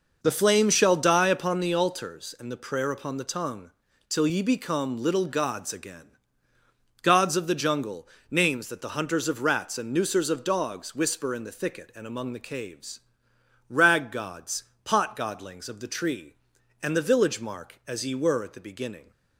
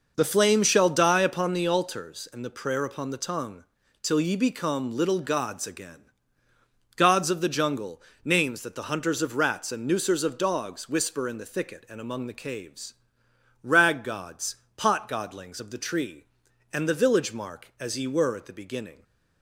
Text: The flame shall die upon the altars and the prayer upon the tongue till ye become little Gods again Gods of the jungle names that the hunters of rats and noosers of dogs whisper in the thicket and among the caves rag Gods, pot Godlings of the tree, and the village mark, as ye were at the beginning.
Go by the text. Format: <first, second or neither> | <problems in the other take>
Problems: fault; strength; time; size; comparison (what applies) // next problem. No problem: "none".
neither | pauses between "tongue" and "till"; slight; the same in both // pauses between "again" and "Gods"; noticeable; the same in both // pauses between "jungle" and "names"; slight; the same in both // pauses between "caves" and "rag"; noticeable; the same in both